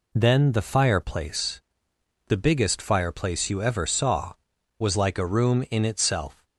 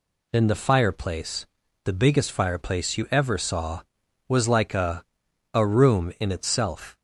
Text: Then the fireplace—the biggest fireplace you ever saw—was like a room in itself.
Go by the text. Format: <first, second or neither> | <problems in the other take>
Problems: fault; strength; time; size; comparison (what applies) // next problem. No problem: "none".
first | says "a" twice; at 5.5 s